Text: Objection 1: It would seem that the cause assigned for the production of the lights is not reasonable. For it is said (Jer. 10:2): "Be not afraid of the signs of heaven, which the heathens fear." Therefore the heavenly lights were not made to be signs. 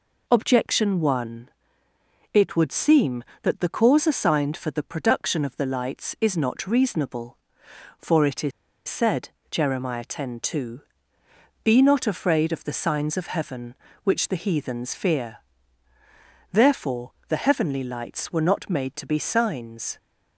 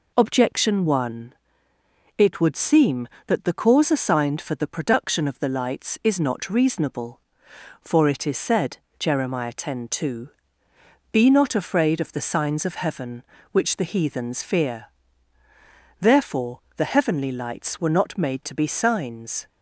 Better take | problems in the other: second | pauses between "is" and "said"; at 8.5 s; 0.36 s long

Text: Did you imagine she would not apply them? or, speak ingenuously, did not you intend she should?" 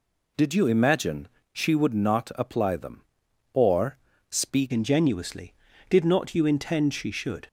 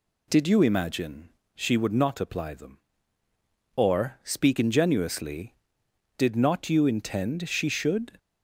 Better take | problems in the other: second | pauses between "imagine" and "she"; slight; at 1.2 s; 0.24 s long; slight in the second // changes voice at "ingenuously"; from 4.7 s on; 2.7 s long

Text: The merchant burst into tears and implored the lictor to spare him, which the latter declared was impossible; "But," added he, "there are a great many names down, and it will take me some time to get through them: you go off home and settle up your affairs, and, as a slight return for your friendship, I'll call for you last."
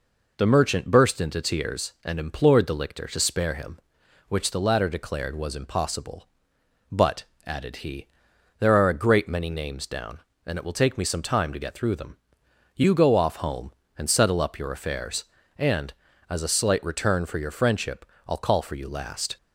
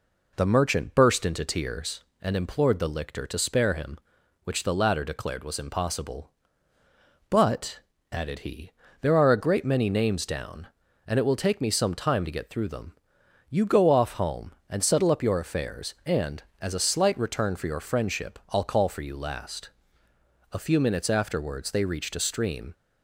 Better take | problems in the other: first | goes on to say "A few minutes afterwards they reached a stream"; strong; from 20.5 s on; 2.2 s long

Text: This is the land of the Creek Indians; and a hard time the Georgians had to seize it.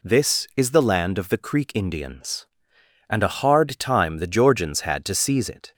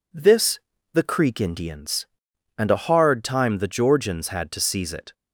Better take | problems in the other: first | skips "is the land of"; at 0.7 s

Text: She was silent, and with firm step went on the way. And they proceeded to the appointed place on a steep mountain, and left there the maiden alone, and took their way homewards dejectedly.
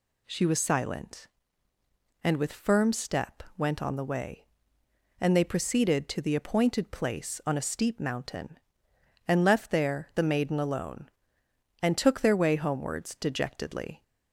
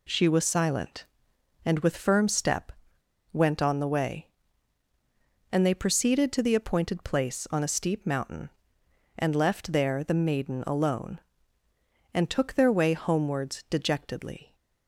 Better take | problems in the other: first | pauses between "step" and "went"; noticeable; at 2.7 s; 0.61 s long

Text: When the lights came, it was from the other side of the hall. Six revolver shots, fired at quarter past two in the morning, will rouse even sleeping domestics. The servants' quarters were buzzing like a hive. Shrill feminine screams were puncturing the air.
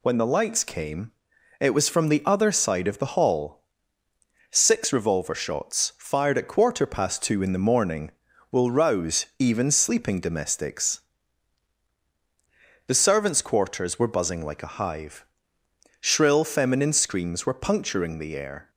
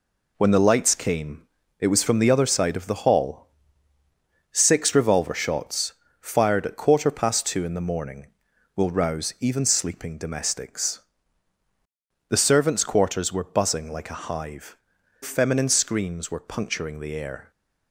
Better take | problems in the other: first | skips "Shrill"; at 14.9 s

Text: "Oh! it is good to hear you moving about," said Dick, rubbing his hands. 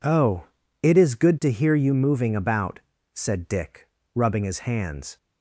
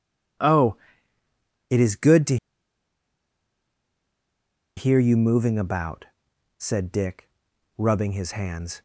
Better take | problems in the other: first | pauses between "to" and "hear"; strong; at 2.3 s; 2.4 s long

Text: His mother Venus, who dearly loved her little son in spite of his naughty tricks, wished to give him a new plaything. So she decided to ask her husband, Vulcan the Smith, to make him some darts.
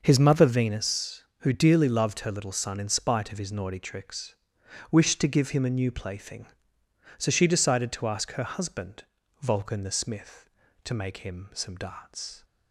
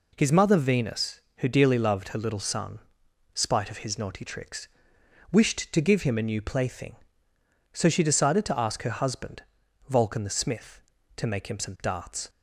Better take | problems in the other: first | skips "in"; at 3.0 s

